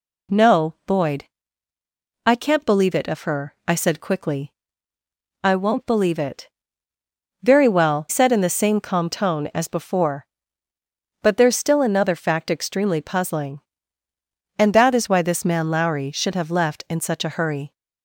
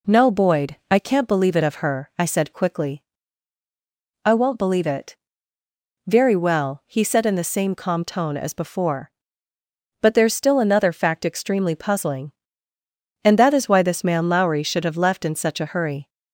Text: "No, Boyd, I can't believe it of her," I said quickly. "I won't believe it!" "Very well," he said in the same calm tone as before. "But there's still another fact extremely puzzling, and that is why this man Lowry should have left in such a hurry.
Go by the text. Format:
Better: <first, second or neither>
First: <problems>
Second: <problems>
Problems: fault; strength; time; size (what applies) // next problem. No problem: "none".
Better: second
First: skips "he"; at 8.0 s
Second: none